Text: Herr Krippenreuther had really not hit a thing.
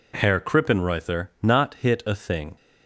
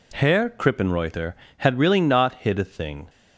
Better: second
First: skips "had really"; at 1.3 s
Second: none

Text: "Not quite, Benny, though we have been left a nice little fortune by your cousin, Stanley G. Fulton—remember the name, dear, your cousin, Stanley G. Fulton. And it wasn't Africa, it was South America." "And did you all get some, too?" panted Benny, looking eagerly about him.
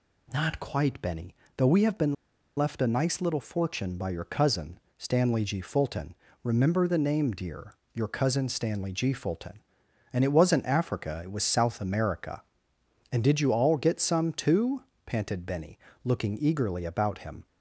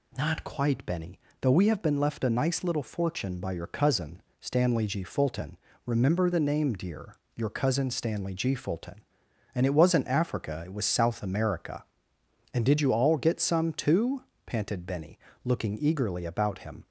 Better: second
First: pauses between "been" and "left"; at 2.1 s; 0.42 s long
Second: none

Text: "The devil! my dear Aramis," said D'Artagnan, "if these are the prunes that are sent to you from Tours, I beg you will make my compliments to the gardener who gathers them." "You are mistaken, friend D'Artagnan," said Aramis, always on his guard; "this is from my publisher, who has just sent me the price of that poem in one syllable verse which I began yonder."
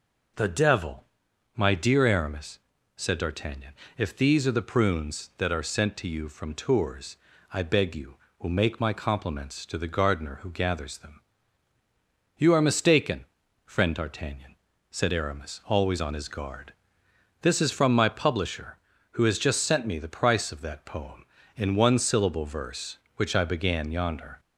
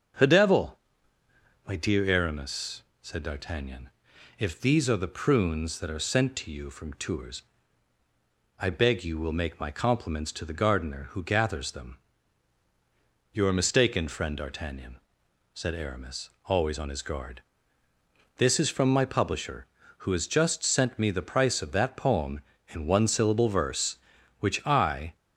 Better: first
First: none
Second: starts louder than the rest; until 2.0 s; 6.5 dB // stops before "began yonder"; at 25.1 s

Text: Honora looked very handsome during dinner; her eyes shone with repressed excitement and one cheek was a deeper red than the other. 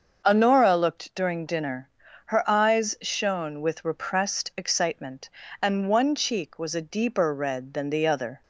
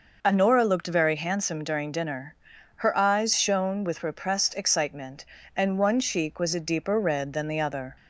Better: second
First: starts louder than the rest; until 1.2 s; 6.5 dB // skips "very handsome"; at 1.1 s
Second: none

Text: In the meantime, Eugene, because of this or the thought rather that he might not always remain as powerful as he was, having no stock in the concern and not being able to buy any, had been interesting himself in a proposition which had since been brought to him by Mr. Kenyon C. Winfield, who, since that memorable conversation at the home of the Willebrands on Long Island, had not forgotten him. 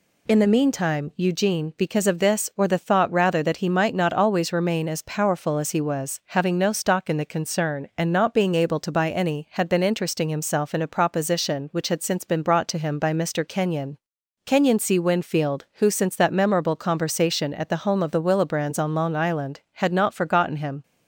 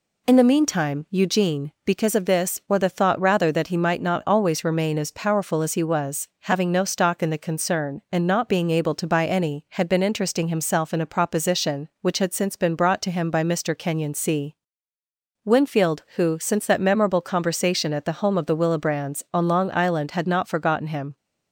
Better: second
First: says "Kenyon" twice; at 14.4 s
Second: none

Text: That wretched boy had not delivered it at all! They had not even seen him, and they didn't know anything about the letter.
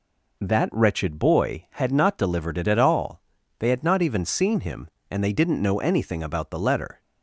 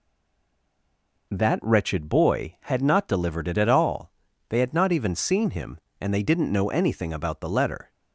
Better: first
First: none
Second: stays silent before the first word; noticeable; until 1.2 s; 1.2 s long

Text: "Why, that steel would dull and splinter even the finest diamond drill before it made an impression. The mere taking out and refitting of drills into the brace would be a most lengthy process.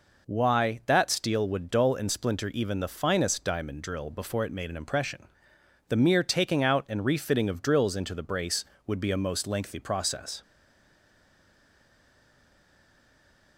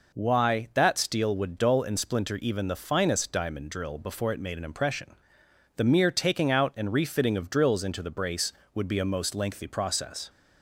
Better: second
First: stays silent after the last word; strong; from 10.4 s on; 3.1 s long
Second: none

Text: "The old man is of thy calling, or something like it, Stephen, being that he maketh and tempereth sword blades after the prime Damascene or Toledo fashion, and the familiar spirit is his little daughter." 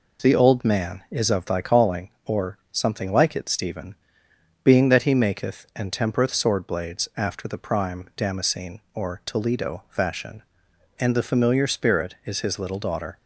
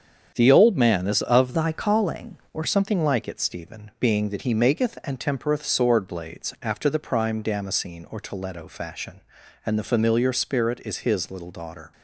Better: first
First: none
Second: starts louder than the rest; strong; until 1.3 s; 7.5 dB // changes voice from "thy" to "or"; from 1.5 to 2.6 s; 1.1 s long

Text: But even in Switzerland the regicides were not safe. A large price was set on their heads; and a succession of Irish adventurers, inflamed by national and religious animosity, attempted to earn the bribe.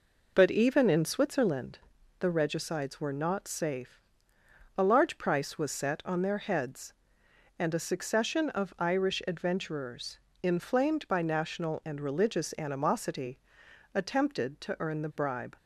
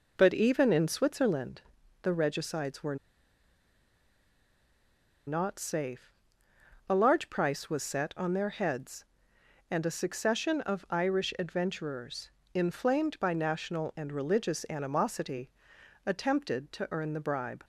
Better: first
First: pauses between "Switzerland" and "the"; at 1.7 s; 0.40 s long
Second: pauses between "Switzerland" and "the"; at 1.6 s; 0.40 s long // pauses between "were" and "not"; strong; at 2.9 s; 2.3 s long

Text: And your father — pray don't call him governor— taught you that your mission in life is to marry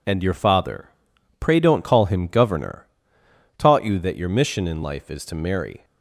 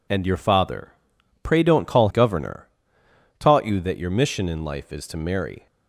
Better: first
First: none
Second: skips "him"; at 2.0 s

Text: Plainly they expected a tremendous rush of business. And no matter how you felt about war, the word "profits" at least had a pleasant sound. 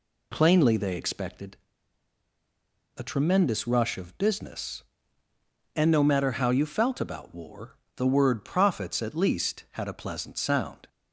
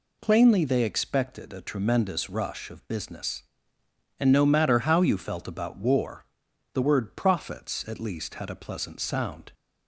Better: second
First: pauses between "expected" and "a"; strong; at 1.5 s; 1.4 s long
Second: none

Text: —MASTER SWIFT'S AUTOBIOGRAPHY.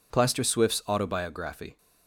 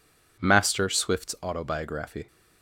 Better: second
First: says "Plaster" for "MASTER"; at 0.1 s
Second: none

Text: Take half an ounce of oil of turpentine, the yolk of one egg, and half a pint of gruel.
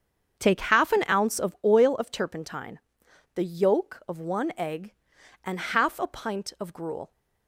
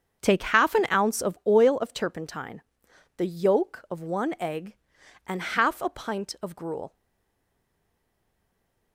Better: first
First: starts louder than the rest; strong; until 1.4 s; 7 dB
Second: starts louder than the rest; until 1.2 s; 7 dB // stays silent after the last word; noticeable; from 6.9 s on; 2.0 s long

